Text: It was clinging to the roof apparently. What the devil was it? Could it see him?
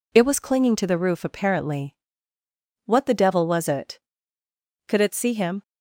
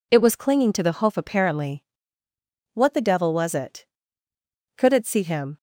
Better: first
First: none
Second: says "hoof" for "roof"; at 0.9 s

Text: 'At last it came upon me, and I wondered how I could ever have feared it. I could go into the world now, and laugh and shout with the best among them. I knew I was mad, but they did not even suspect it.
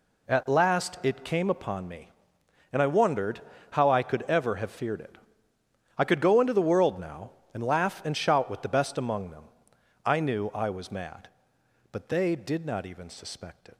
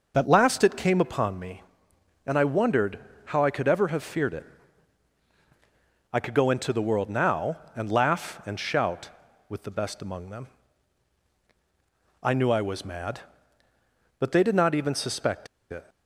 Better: first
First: pauses between "wondered" and "how"; slight; at 3.3 s; 0.32 s long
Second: pauses between "wondered" and "how"; slight; at 2.9 s; 0.28 s long // pauses between "suspect" and "it"; slight; at 15.4 s; 0.25 s long

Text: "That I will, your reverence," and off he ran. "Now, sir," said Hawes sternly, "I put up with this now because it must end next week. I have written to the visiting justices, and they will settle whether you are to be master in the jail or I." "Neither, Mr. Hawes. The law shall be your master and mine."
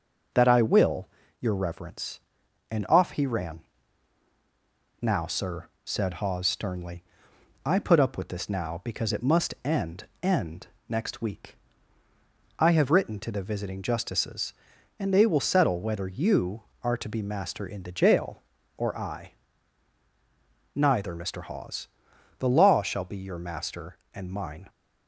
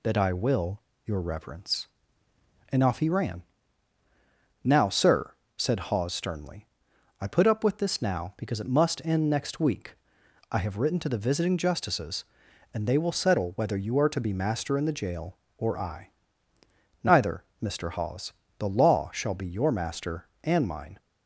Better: second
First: says "end" twice; at 10.2 s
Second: none

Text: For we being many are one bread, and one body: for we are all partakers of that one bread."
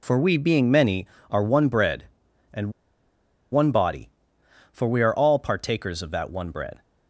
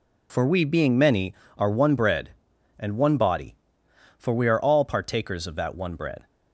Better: second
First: pauses between "and" and "one"; noticeable; at 2.6 s; 0.82 s long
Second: none

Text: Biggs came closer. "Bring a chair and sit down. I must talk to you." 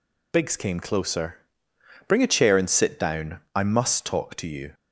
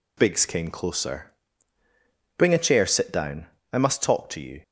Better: first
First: none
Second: skips "and"; at 2.8 s

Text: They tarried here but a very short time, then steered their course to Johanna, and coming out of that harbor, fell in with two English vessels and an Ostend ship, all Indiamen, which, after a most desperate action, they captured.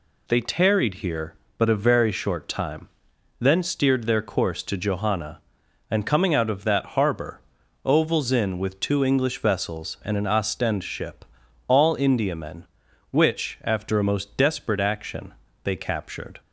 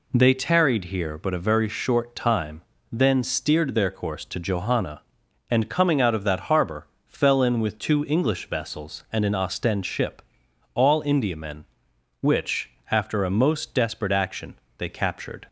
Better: second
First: says "ovals" for "fell"; at 7.8 s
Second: none

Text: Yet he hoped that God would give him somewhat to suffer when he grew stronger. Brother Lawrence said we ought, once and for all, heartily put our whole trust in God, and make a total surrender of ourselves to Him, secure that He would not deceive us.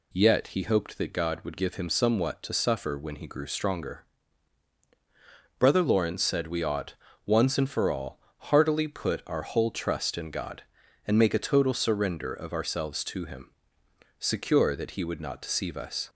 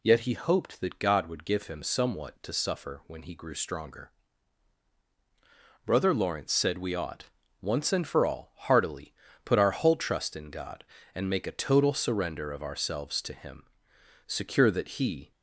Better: first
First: none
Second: pauses between "heartily" and "put"; slight; at 9.1 s; 0.30 s long // stops before "would not deceive us"; at 15.3 s

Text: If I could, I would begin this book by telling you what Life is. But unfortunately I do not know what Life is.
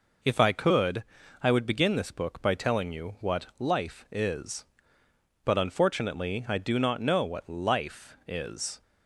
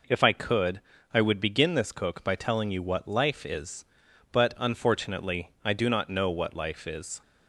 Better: first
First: none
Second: says "cook" for "book"; at 1.9 s

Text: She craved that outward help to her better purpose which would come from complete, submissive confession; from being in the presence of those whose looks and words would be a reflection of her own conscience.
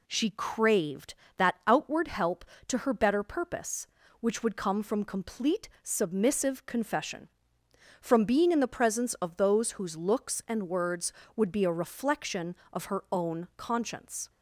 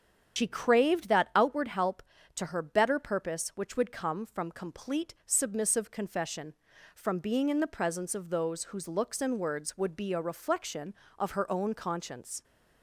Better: first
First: none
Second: loses the start of "She"; at 0.3 s; 90 ms // starts louder than the rest; strong; until 1.4 s; 8 dB

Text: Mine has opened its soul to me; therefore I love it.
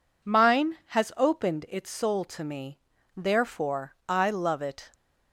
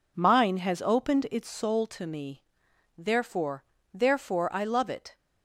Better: first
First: none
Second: says "therefore" twice; at 3.9 s

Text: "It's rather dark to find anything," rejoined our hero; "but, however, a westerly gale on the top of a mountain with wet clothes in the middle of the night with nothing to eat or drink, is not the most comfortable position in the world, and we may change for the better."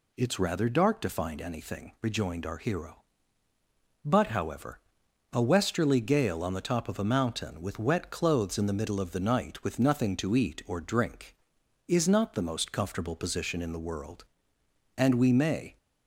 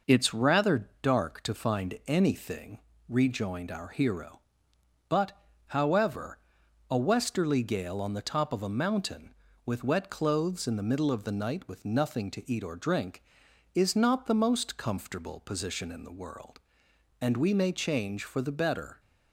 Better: second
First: stops before "change for the better"; at 15.7 s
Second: none

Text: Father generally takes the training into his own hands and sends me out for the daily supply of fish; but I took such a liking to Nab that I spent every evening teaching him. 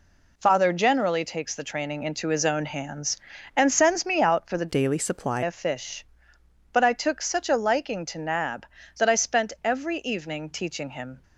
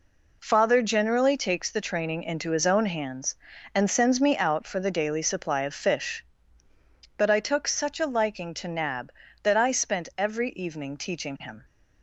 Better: second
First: changes voice from "daily" to "supply"; from 4.6 to 5.4 s; 0.8 s long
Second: none

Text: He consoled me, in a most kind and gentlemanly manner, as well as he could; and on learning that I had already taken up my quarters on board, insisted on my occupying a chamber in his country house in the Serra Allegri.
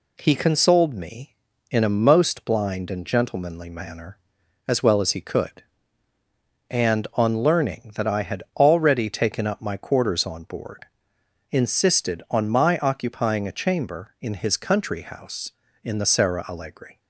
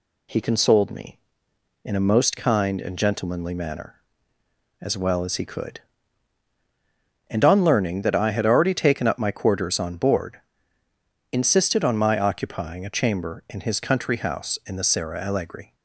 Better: second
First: says "blind" for "kind"; at 2.4 s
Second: none

